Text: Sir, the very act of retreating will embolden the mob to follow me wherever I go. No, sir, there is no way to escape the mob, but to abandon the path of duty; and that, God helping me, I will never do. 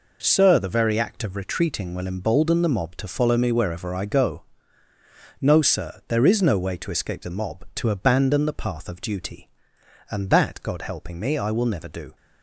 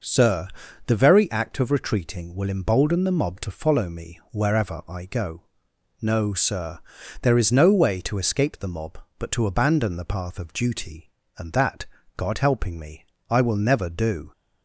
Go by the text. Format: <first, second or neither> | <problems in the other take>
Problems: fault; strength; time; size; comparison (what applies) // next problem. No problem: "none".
second | skips "but"; at 7.7 s